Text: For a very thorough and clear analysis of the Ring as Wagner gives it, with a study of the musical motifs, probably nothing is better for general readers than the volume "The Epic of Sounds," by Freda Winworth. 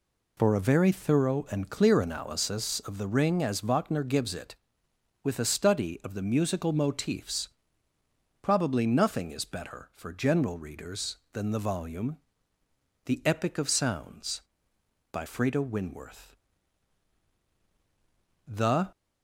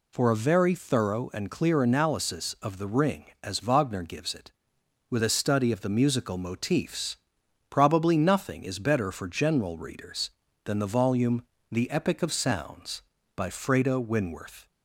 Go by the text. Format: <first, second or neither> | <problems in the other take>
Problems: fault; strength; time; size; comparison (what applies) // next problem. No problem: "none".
second | pauses between "volume" and "The"; noticeable; at 12.1 s; 0.86 s long; slight in the second // goes on to say "The"; slight; from 18.4 s on; 0.44 s long